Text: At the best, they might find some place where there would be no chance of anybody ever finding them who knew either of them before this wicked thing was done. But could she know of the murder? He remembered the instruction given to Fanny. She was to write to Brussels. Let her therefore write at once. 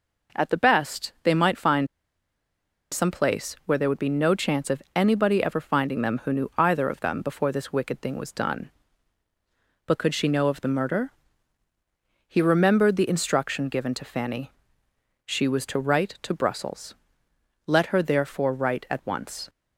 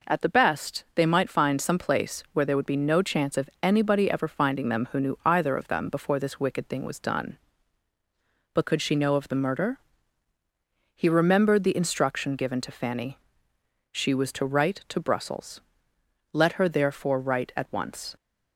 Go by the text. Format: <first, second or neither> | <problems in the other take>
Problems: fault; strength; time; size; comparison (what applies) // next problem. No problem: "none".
second | pauses between "find" and "some"; at 1.8 s; 1.0 s long